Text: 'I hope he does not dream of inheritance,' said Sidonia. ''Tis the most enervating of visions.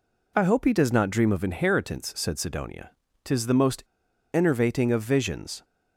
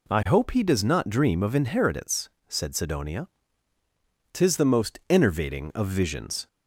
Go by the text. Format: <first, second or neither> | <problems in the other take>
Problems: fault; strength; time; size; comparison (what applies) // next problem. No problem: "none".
second | pauses between "most" and "enervating"; noticeable; at 3.8 s; 0.48 s long